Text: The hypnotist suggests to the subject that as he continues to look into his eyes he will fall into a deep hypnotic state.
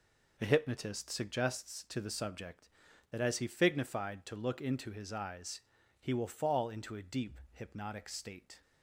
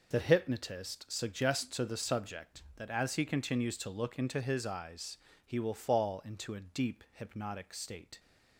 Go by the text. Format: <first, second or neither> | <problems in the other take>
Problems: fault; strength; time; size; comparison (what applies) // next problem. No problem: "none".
second | says "fignified" for "continues"; at 3.4 s // pauses between "eyes" and "he"; at 5.6 s; 0.38 s long; slight in the second